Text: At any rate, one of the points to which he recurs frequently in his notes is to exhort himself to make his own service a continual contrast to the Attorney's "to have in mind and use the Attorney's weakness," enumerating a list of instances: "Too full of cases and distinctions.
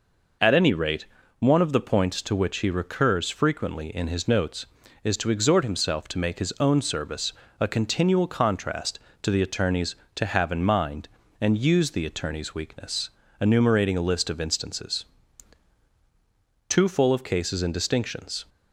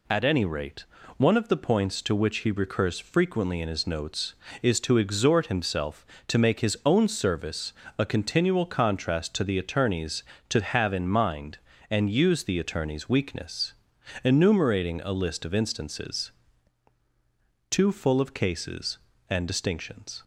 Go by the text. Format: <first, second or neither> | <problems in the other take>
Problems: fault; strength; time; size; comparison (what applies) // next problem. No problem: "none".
neither | pauses between "service" and "a"; slight; the same in both